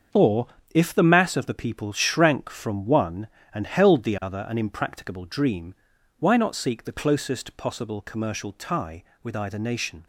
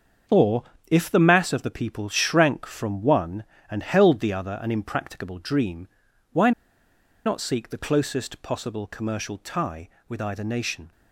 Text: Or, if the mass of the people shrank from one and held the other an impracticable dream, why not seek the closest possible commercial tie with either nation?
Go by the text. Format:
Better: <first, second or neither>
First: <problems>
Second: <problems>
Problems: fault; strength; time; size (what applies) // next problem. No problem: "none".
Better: first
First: starts louder than the rest; until 1.3 s; 7 dB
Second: starts louder than the rest; until 1.5 s; 7 dB // pauses between "why" and "not"; noticeable; at 6.5 s; 0.74 s long